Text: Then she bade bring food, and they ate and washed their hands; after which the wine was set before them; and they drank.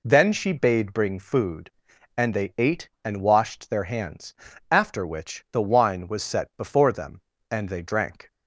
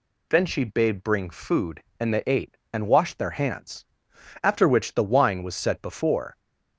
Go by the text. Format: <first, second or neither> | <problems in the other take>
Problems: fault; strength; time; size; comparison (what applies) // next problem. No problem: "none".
first | stops before "them and they drank"; at 6.3 s